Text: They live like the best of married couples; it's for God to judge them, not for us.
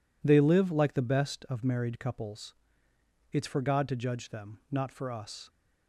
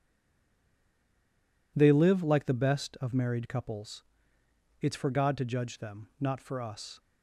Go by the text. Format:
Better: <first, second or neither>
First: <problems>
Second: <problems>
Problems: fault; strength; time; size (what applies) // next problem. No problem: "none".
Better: first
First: none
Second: stays silent before the first word; noticeable; until 1.7 s; 1.7 s long